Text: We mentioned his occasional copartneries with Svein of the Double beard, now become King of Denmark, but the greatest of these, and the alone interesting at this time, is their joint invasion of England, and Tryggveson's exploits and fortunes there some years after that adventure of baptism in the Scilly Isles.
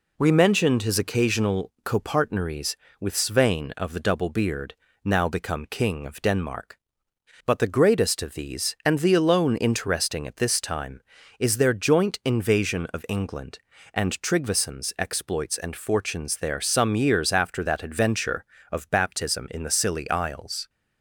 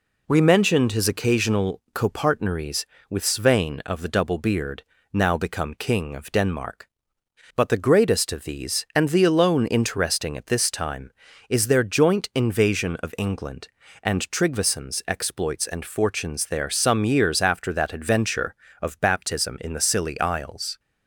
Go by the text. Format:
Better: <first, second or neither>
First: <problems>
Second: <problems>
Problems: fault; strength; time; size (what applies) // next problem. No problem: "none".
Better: neither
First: none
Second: none